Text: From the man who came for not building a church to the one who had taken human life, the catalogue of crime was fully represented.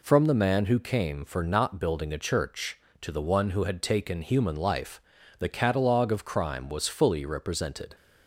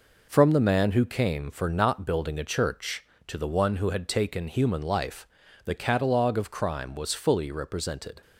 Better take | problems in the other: first | gets quieter; noticeable; throughout; 5.5 dB

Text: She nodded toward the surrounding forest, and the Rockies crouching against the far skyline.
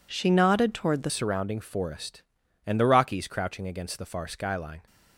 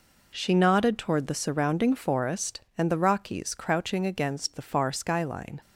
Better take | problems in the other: second | changes voice at "surrounding"; from 1.0 s on; 3.8 s long

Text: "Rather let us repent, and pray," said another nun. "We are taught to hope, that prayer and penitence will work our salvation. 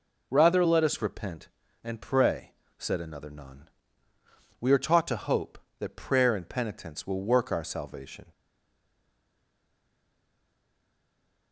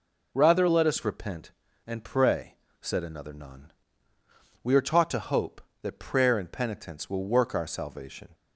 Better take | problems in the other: second | stays silent after the last word; strong; from 8.3 s on; 3.2 s long

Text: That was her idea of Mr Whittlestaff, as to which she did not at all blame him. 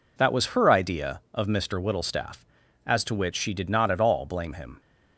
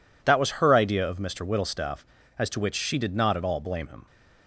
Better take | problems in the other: neither | none

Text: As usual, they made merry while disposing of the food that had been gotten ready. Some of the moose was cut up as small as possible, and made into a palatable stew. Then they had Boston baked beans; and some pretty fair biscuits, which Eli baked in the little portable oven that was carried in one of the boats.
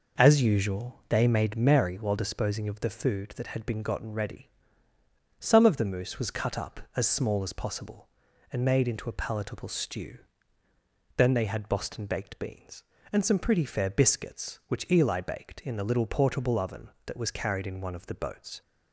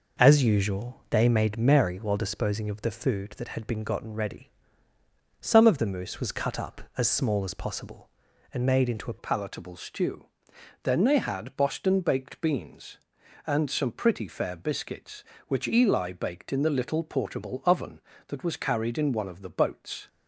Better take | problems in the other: first | changes voice at "palatable"; from 9.1 s on; 10.9 s long

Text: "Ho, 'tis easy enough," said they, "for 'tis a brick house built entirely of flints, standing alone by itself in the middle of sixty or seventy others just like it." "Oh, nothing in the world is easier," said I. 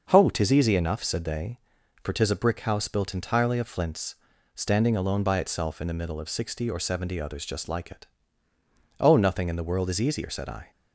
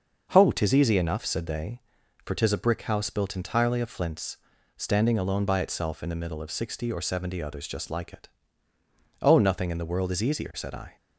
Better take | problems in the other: neither | starts louder than the rest; noticeable; the same in both

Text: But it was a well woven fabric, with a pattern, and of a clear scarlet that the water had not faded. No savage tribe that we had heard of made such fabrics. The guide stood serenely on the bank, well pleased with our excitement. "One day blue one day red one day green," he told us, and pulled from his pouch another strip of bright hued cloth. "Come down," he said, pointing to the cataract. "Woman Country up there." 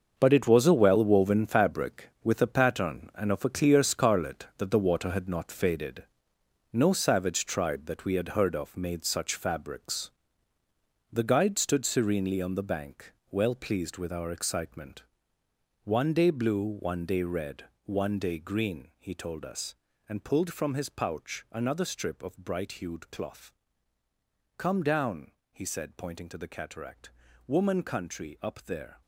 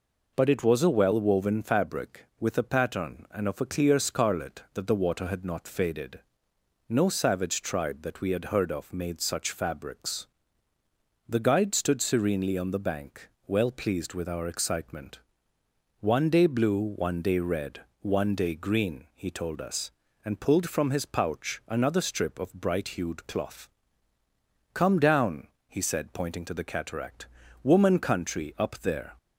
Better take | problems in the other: second | gets quieter; strong; throughout; 11.5 dB // pauses between "red" and "one"; slight; at 17.6 s; 0.20 s long; slight in the second

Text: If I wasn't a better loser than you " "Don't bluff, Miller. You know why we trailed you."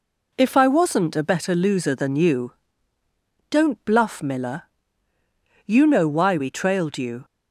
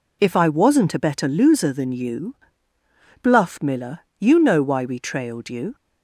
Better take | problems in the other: first | skips "Don't"; at 3.2 s

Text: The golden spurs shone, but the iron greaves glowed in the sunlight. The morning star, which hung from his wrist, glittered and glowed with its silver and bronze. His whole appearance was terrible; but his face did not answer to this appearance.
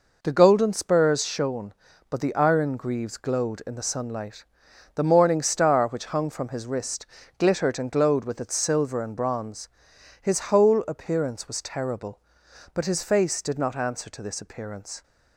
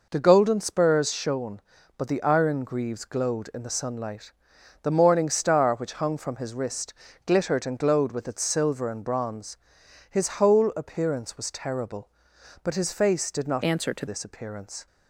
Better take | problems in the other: first | changes voice from "answer" to "to"; from 13.6 to 14.0 s; 0.4 s long

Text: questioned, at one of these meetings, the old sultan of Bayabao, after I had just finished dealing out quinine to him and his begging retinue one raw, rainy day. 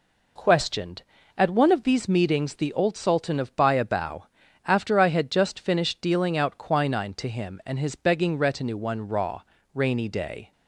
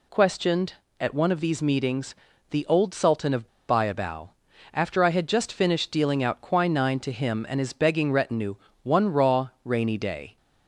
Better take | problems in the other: first | pauses between "of" and "Bayabao"; slight; at 3.4 s; 0.21 s long // pauses between "retinue" and "one"; slight; at 8.5 s; 0.28 s long

